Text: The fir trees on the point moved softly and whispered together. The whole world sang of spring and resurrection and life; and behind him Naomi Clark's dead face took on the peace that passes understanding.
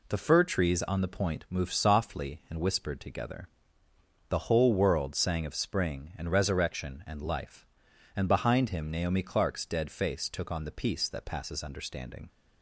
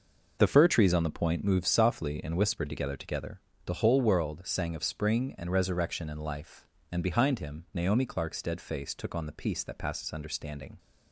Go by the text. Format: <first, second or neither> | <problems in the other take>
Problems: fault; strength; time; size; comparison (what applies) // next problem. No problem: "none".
first | says "together" twice; at 2.9 s